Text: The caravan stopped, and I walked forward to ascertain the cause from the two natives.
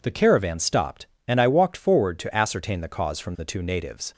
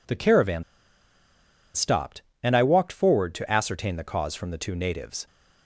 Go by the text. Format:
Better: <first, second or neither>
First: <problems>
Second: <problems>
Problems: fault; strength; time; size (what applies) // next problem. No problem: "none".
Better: first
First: none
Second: pauses between "caravan" and "stopped"; at 0.6 s; 1.1 s long